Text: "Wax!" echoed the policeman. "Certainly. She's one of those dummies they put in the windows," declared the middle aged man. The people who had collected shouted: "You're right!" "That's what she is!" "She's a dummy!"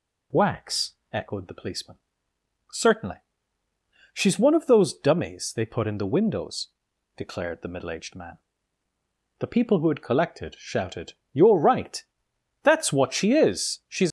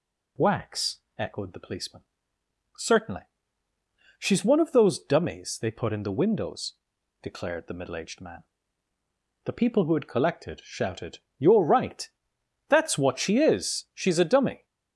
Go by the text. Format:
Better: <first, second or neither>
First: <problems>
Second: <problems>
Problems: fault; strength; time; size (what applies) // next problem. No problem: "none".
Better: second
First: stops before "a dummy"; at 14.0 s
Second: none